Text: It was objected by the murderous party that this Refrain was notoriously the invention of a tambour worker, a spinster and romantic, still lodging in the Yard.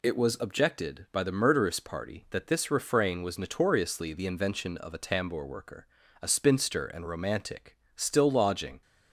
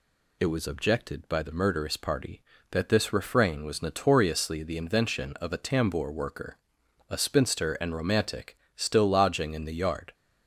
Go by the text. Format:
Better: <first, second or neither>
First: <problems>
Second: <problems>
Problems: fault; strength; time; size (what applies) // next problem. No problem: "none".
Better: second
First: stops before "in the Yard"; at 8.8 s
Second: none